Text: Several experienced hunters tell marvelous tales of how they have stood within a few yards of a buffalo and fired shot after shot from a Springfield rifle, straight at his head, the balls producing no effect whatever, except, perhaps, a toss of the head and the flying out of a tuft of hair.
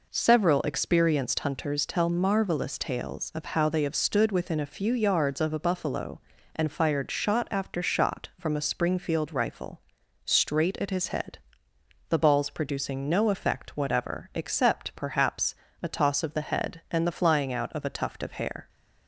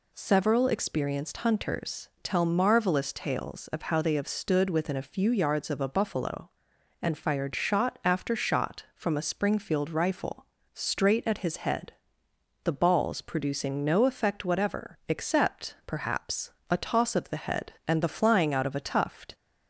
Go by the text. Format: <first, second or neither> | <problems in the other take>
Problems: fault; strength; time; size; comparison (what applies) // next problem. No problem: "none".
first | stops before "of hair"; at 19.3 s